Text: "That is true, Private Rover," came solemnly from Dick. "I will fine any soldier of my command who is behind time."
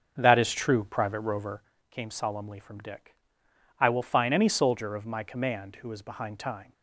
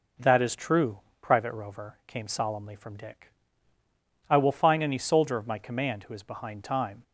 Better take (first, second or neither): second